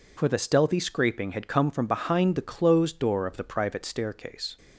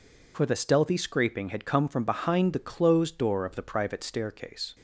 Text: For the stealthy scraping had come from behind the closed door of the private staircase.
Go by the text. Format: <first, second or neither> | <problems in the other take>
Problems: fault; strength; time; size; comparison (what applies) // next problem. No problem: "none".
neither | none